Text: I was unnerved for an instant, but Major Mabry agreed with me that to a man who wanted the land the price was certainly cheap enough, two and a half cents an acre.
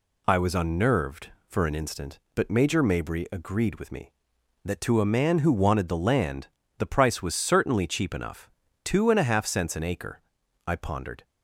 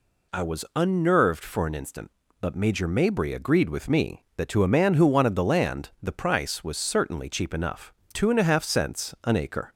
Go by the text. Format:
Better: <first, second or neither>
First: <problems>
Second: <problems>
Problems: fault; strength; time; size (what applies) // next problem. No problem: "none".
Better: second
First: pauses between "land" and "the"; slight; at 6.4 s; 0.32 s long // goes on to say "I pondered"; from 10.6 s on; 0.58 s long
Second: none